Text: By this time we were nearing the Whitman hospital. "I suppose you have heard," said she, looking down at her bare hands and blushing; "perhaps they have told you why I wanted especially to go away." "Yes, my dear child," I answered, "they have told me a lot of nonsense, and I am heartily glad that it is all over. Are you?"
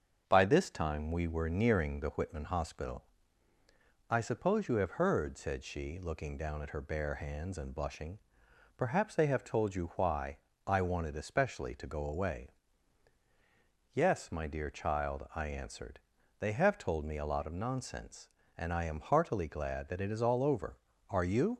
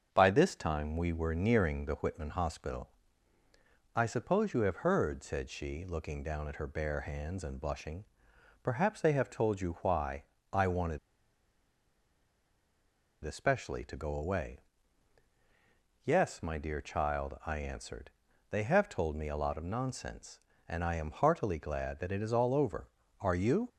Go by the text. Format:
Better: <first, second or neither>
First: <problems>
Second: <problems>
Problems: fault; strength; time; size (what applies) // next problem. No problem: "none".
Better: first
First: starts louder than the rest; until 1.2 s; 7 dB // pauses between "why" and "I"; slight; at 10.3 s; 0.28 s long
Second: starts louder than the rest; until 1.1 s; 7 dB // pauses between "why" and "I"; slight; at 10.2 s; 0.28 s long // pauses between "wanted" and "especially"; strong; at 10.9 s; 2.2 s long